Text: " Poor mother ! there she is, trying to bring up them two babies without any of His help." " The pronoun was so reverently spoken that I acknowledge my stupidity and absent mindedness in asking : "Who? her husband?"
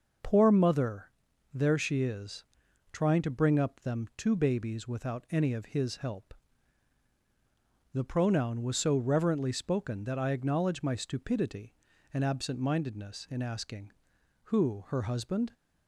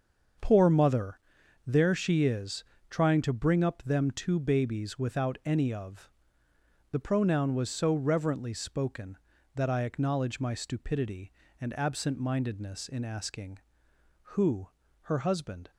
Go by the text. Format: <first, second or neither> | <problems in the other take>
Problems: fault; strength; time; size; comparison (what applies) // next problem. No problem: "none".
first | starts louder than the rest; strong; until 1.8 s; 7 dB; also in the first // skips "His help"; at 6.2 s